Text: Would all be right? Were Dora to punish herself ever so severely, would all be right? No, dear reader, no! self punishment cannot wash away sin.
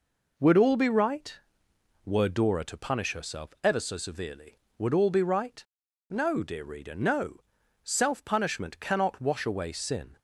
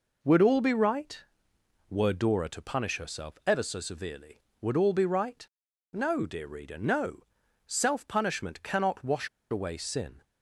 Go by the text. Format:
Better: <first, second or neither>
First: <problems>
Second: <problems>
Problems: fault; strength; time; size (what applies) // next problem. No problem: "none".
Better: first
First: none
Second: pauses between "wash" and "away"; slight; at 9.2 s; 0.22 s long